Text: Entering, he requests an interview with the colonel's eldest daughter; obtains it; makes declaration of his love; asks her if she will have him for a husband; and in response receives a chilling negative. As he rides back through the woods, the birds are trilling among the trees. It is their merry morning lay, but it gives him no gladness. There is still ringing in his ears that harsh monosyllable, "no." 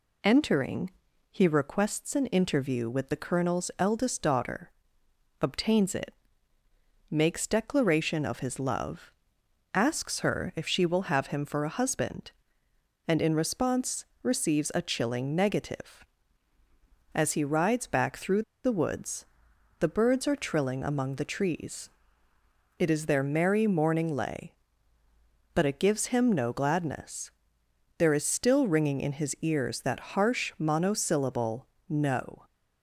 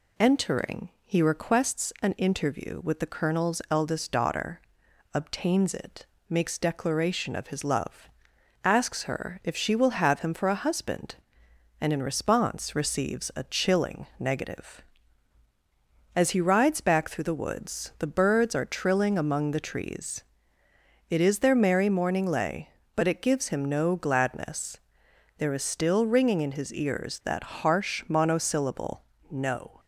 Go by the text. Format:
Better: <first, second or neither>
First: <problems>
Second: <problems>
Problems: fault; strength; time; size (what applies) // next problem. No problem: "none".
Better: second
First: pauses between "response" and "receives"; slight; at 14.0 s; 0.18 s long // pauses between "through" and "the"; slight; at 18.4 s; 0.22 s long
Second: none